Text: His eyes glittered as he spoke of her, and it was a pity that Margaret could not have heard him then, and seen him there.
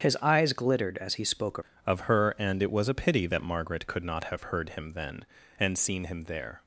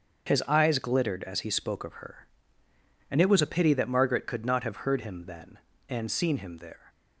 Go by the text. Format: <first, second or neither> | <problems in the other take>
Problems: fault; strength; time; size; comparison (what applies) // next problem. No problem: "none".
second | starts louder than the rest; strong; until 1.0 s; 7.5 dB; also in the second // changes voice at "of"; from 1.8 s on; 4.8 s long